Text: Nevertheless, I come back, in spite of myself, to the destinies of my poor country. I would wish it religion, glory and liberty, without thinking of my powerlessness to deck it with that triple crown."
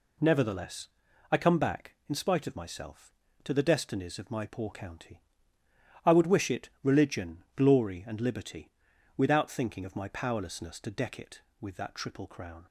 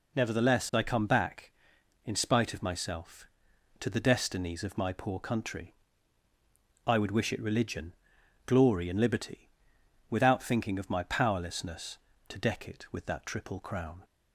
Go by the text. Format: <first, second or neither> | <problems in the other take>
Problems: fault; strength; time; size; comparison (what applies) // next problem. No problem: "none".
second | says "county" for "country"; at 4.7 s